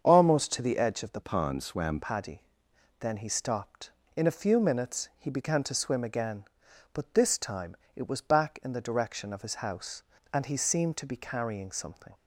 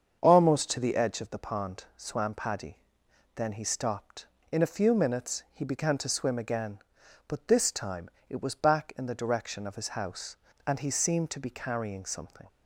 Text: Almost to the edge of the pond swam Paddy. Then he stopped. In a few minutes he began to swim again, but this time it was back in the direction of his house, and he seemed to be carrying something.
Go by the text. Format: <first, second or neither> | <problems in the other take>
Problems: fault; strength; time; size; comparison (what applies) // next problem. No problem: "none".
second | starts louder than the rest; strong; until 1.0 s; 7 dB; strong in the second // changes voice from "pond" to "swam"; from 1.2 to 1.9 s; 0.7 s long // pauses between "time" and "it"; slight; at 7.7 s; 0.22 s long; slight in the second